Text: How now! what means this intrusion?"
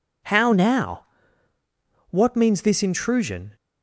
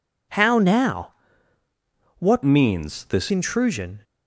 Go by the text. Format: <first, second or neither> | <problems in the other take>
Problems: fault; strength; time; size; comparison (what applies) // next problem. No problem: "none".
first | changes voice from "means" to "this"; from 2.4 to 3.3 s; 0.9 s long